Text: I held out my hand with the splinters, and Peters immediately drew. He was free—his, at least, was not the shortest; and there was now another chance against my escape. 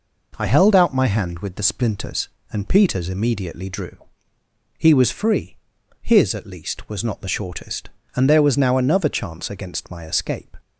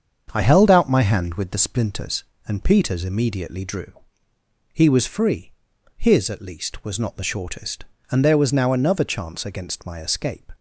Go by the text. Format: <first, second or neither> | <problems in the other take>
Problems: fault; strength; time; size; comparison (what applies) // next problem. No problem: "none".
first | starts louder than the rest; until 1.7 s; 7 dB